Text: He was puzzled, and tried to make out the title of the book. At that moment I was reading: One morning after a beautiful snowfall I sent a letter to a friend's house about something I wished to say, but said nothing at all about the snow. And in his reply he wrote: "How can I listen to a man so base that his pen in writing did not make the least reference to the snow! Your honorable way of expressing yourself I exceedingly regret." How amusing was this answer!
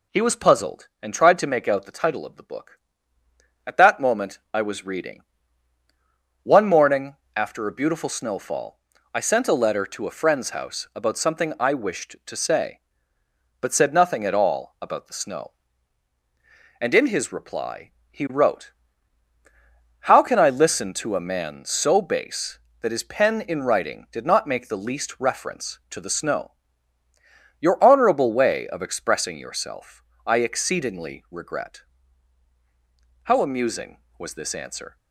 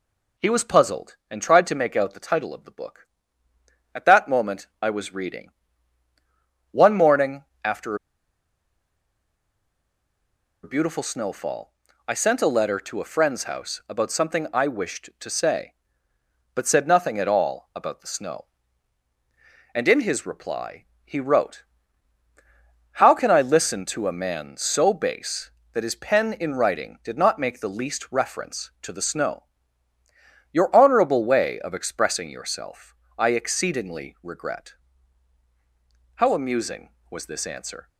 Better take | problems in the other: first | pauses between "moment" and "I"; slight; at 4.6 s; 0.16 s long; slight in the first // pauses between "morning" and "after"; slight; at 7.4 s; 0.20 s long; slight in the first // pauses between "after" and "a"; strong; at 7.9 s; 2.6 s long // pauses between "snowfall" and "I"; slight; at 11.7 s; 0.34 s long; slight in the first // pauses between "reply" and "he"; slight; at 20.8 s; 0.20 s long; slight in the first // pauses between "yourself" and "I"; slight; at 32.9 s; 0.24 s long; slight in the first

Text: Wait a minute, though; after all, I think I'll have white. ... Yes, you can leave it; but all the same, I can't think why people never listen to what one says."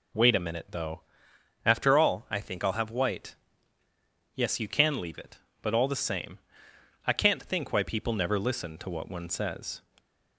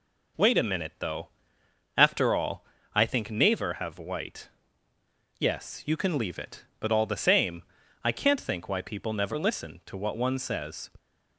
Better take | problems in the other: first | says "Naver" for "I'll"; at 3.3 s

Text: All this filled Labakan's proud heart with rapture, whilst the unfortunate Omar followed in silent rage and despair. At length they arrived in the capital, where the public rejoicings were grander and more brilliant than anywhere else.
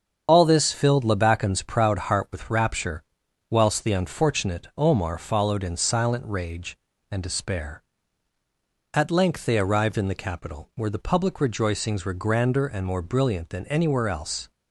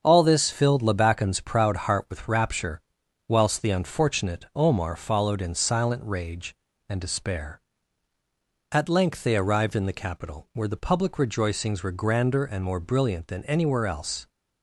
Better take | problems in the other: second | loses the start of "All"; at 0.2 s; 25 ms // starts louder than the rest; strong; until 1.2 s; 7 dB; also in the second

